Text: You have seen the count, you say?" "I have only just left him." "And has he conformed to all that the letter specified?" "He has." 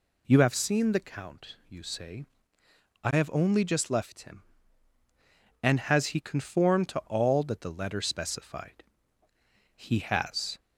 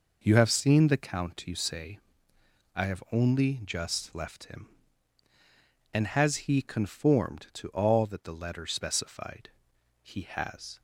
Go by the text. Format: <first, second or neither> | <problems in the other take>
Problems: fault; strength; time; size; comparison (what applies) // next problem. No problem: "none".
neither | none